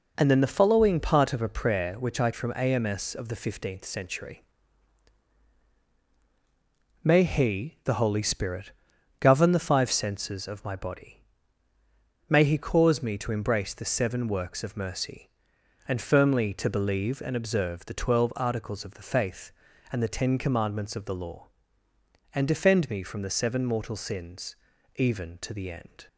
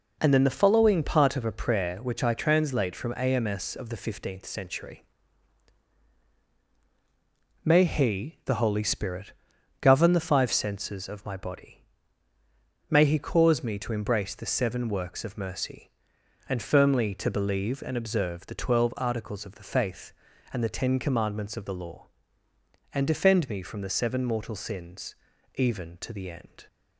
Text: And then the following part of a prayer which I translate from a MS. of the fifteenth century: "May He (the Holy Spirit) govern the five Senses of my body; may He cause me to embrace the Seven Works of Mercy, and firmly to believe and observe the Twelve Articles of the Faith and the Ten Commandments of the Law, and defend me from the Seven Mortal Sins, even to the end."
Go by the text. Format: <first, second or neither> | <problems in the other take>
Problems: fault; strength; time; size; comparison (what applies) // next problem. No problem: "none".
second | skips "translate"; at 2.3 s